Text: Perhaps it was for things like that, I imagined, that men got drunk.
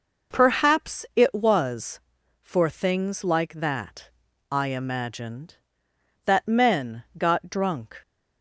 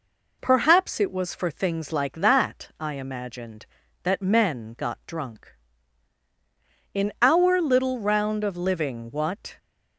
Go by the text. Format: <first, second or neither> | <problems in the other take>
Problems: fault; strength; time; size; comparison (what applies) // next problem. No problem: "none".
first | goes on to say "In our little round of living what"; strong; from 6.9 s on; 2.6 s long